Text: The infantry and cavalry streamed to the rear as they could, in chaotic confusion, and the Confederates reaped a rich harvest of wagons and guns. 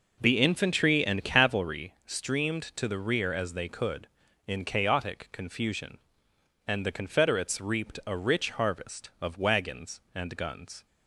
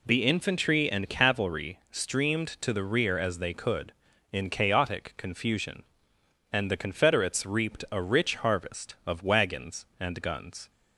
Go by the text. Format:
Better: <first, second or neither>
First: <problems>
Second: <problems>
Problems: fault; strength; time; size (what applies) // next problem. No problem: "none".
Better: second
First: starts louder than the rest; noticeable; until 1.7 s; 5 dB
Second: none